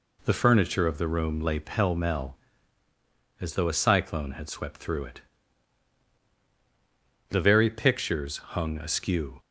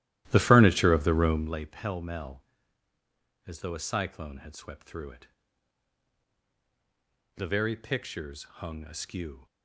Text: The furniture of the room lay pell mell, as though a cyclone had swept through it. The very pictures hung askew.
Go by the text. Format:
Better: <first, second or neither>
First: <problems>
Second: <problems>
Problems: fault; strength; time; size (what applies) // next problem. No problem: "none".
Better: first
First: none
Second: starts louder than the rest; strong; until 1.6 s; 14 dB